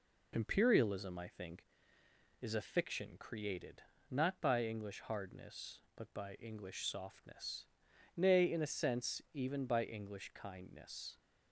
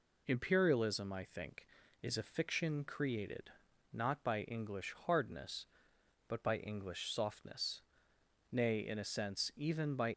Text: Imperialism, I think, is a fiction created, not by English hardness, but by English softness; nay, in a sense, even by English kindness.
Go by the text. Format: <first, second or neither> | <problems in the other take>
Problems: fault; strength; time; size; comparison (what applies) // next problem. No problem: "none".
first | stops before "English kindness"; at 10.1 s